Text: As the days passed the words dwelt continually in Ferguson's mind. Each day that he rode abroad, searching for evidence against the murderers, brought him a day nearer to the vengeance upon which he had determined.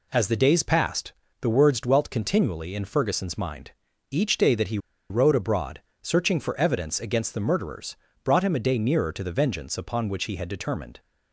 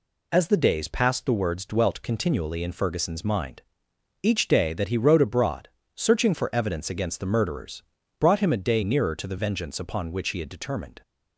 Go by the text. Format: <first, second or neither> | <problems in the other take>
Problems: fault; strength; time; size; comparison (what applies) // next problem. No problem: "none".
second | pauses between "passed" and "the"; slight; at 1.1 s; 0.30 s long // pauses between "he" and "rode"; slight; at 4.7 s; 0.31 s long